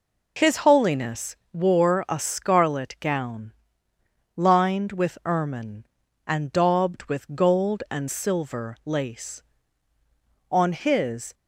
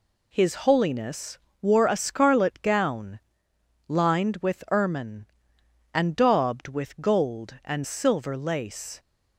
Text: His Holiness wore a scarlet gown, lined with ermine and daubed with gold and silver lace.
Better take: second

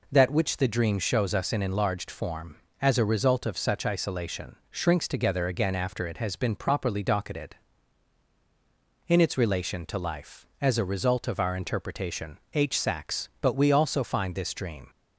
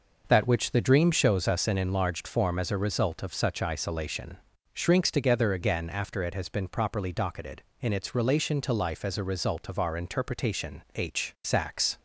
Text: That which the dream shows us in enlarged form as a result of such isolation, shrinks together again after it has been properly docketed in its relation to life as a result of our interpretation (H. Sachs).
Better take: second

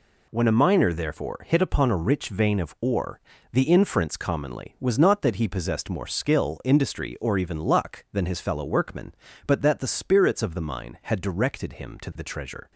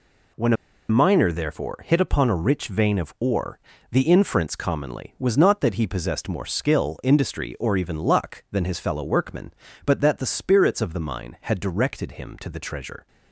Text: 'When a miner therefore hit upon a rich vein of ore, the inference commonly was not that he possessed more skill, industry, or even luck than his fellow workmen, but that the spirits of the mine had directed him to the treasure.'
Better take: first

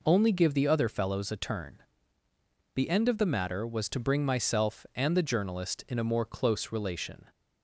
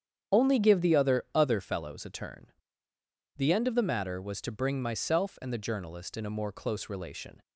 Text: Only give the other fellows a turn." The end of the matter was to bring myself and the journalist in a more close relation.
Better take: first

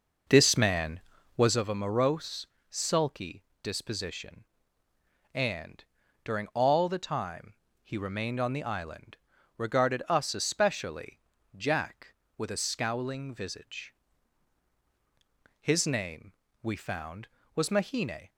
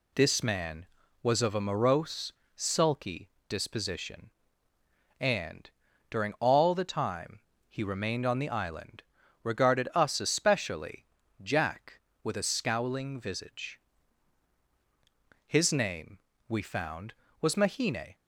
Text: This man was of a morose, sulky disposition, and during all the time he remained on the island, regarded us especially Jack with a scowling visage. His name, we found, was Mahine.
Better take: second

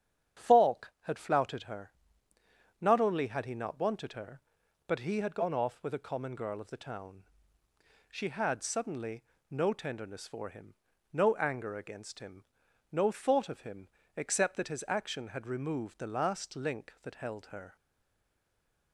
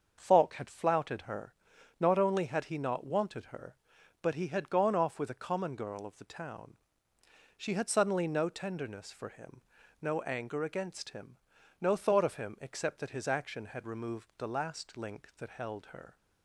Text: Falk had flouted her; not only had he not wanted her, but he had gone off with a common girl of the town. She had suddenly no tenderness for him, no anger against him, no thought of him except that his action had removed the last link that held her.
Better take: second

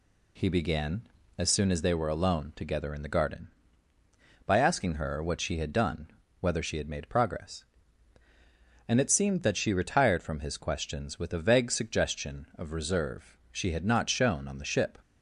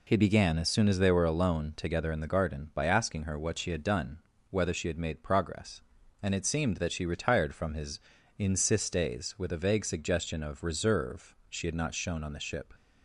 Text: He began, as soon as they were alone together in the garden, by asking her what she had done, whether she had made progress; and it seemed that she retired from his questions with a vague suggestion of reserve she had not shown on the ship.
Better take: first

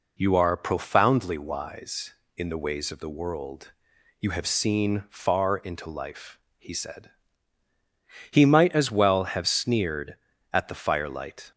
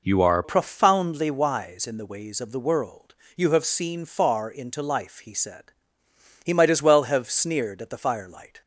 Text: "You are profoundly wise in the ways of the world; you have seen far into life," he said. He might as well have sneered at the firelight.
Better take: first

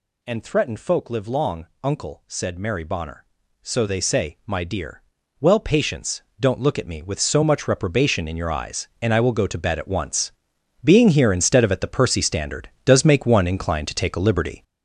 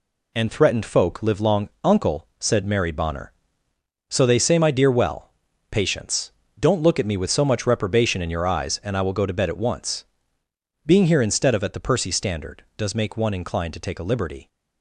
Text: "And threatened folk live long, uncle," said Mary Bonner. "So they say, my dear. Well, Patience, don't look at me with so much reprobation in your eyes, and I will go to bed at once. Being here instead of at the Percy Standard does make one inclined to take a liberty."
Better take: second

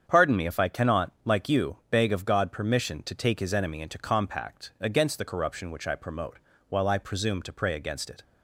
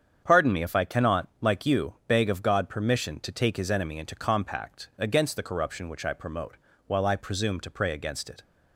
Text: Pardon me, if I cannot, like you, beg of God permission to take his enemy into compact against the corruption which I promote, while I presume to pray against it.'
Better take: neither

